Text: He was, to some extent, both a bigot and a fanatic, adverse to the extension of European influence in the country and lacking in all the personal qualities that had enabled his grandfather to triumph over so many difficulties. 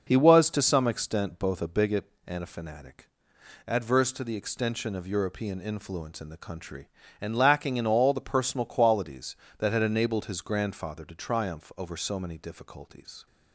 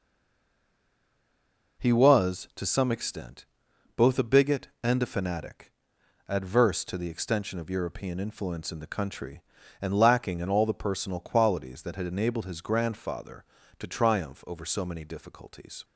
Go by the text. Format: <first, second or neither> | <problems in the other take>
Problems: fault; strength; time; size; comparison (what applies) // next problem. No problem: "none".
first | stays silent before the first word; noticeable; until 1.7 s; 1.7 s long